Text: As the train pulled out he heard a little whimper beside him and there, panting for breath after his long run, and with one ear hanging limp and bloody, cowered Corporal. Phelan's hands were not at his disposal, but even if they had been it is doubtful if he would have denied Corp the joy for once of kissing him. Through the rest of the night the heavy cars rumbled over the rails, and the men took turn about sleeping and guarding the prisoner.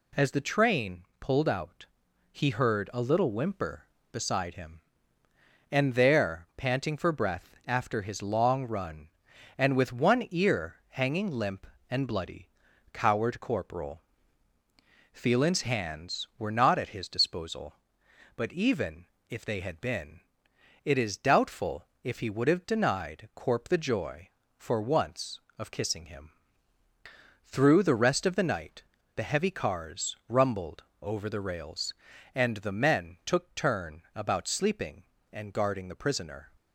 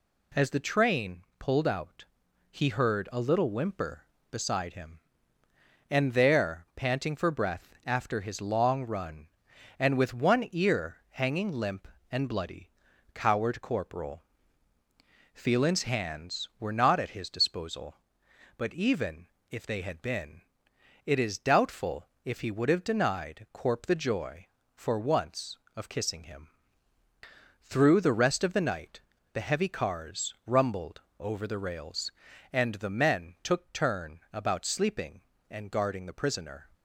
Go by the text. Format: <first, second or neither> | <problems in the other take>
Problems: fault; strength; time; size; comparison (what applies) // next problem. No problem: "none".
neither | pauses between "train" and "pulled"; slight; the same in both // pauses between "out" and "he"; noticeable; the same in both // pauses between "even" and "if"; slight; the same in both // pauses between "been" and "it"; noticeable; the same in both // pauses between "doubtful" and "if"; slight; the same in both // pauses between "night" and "the"; slight; the same in both // pauses between "rumbled" and "over"; slight; the same in both